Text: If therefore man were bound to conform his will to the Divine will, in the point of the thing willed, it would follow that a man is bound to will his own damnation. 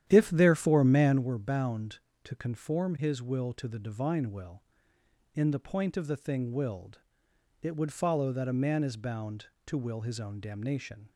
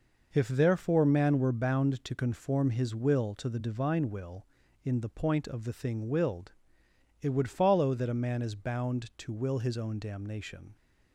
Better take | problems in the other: second | starts louder than the rest; strong; until 1.3 s; 10.5 dB

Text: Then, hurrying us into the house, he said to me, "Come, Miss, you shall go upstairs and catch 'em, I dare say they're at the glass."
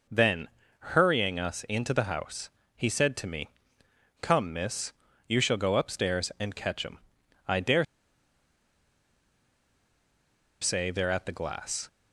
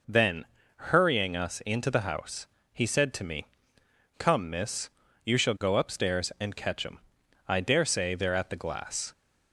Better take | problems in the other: second | pauses between "dare" and "say"; strong; at 7.8 s; 2.7 s long

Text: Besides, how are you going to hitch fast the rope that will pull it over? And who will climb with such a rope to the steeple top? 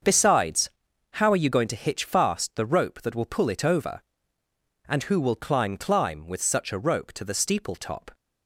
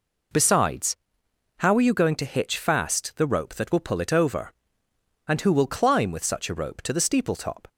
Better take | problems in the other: second | starts louder than the rest; until 1.4 s; 6.5 dB // says "climb" twice; at 5.7 s

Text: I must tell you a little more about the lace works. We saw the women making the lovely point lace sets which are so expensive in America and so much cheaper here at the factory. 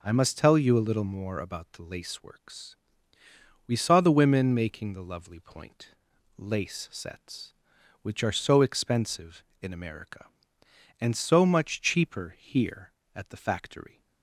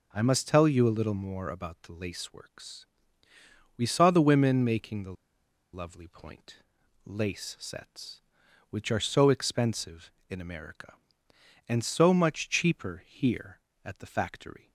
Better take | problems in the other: first | pauses between "the" and "lovely"; noticeable; at 5.1 s; 0.60 s long // pauses between "point" and "lace"; noticeable; at 6.5 s; 0.50 s long; noticeable in the first

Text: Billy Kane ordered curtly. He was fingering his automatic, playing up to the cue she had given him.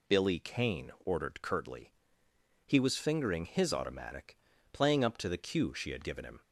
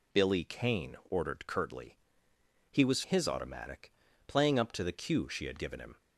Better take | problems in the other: first | skips "fingering"; at 3.0 s

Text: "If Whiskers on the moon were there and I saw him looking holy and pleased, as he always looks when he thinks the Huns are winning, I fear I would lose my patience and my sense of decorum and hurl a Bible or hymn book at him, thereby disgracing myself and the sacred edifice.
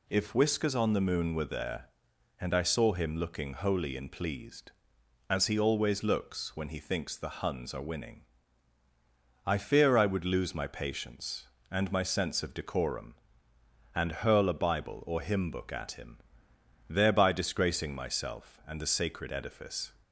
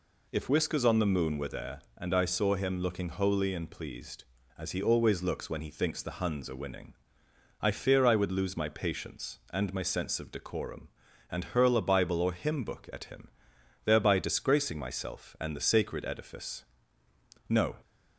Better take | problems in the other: first | goes on to say "No"; slight; from 17.4 s on; 0.30 s long

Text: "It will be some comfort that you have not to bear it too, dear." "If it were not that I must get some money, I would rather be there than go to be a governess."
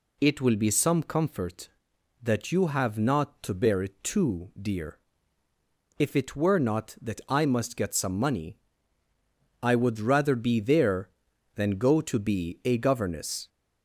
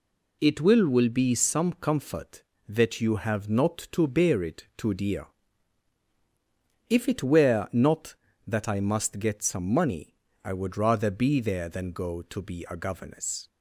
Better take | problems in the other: first | says "will" twice; at 0.8 s

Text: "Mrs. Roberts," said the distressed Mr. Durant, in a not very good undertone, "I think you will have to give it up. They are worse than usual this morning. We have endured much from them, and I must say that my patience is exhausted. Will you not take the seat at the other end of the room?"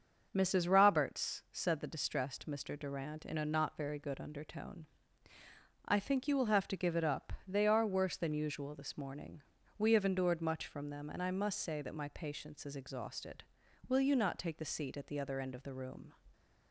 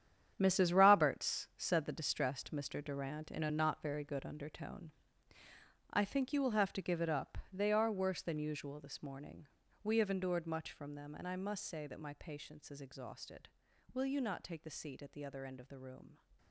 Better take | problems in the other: first | gets quieter; strong; throughout; 11.5 dB // starts louder than the rest; strong; until 1.3 s; 9 dB; also in the first

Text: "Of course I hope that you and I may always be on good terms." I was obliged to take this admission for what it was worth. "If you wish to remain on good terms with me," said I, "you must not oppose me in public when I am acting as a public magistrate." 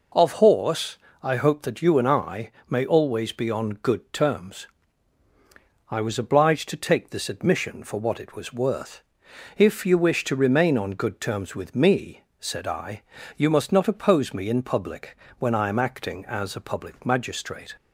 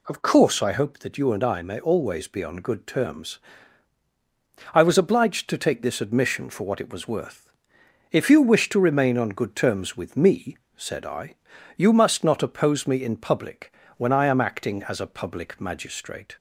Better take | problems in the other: second | says "horse" for "course"; at 0.3 s // pauses between "I" and "may"; slight; at 2.5 s; 0.18 s long // pauses between "public" and "when"; slight; at 15.1 s; 0.24 s long; slight in the second

